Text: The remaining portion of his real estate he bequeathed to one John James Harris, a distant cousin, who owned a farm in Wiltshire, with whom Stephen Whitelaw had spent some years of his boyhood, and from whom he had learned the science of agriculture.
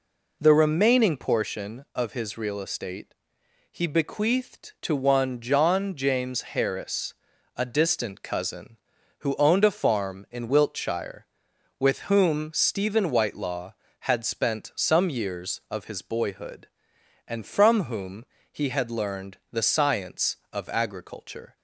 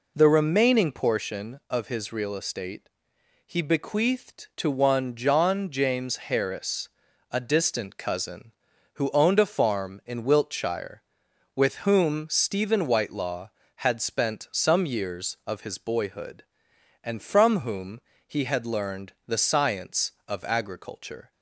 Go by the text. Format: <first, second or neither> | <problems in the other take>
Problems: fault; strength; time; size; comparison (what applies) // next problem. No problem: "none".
neither | pauses between "estate" and "he"; noticeable; the same in both // pauses between "whom" and "he"; slight; the same in both